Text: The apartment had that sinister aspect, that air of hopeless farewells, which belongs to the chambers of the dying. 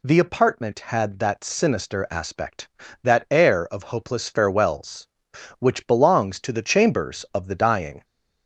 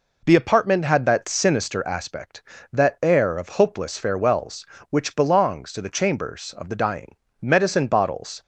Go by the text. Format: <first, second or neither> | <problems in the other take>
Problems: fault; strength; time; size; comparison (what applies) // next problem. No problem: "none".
first | goes on to say "Medicine bottles"; noticeable; from 7.4 s on; 1.0 s long